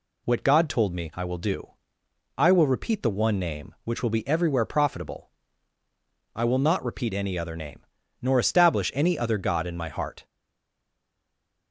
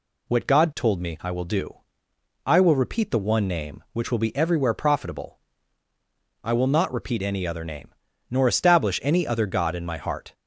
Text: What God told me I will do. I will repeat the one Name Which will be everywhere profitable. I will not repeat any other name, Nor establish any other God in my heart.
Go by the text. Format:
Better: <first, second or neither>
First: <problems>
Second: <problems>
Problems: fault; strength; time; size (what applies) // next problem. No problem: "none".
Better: second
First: stays silent after the last word; noticeable; from 10.2 s on; 1.5 s long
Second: none